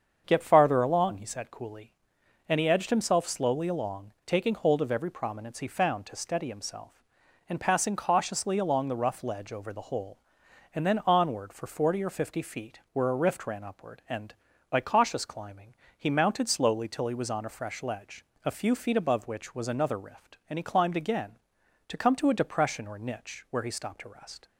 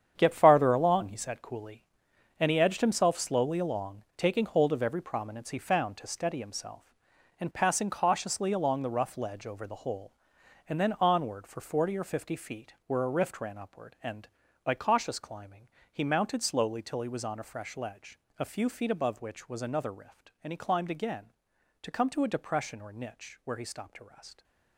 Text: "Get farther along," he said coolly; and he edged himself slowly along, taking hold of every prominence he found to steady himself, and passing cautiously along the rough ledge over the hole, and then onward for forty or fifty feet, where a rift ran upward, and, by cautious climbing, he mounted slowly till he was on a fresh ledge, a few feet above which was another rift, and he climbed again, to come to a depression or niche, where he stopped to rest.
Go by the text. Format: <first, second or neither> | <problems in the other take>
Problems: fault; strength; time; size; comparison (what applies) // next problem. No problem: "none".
first | gets quieter; strong; throughout; 11 dB // starts louder than the rest; strong; until 1.1 s; 8.5 dB; strong in the first